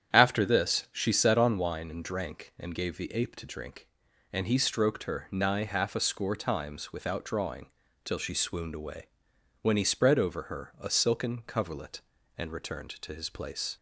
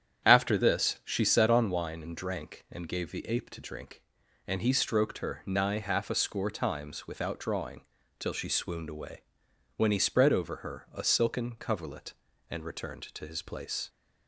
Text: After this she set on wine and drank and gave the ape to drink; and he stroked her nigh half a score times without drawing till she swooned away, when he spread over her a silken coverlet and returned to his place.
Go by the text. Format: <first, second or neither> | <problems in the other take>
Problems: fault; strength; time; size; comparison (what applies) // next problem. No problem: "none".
neither | starts louder than the rest; strong; the same in both // pauses between "drawing" and "till"; slight; the same in both